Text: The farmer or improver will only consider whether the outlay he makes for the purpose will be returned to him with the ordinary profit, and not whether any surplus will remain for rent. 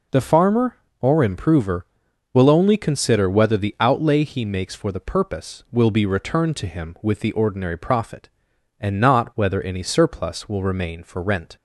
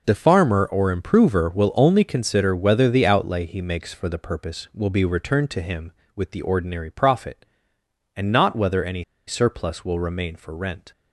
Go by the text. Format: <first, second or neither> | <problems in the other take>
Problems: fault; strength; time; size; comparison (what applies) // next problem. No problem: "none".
first | pauses between "any" and "surplus"; slight; at 9.0 s; 0.25 s long